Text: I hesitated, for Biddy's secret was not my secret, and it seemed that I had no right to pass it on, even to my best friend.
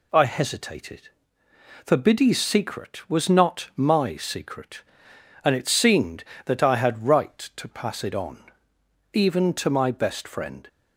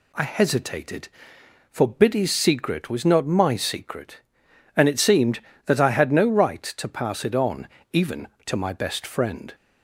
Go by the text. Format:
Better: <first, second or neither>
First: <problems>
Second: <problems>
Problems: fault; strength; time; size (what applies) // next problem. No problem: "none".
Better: second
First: skips "no"; at 7.0 s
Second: none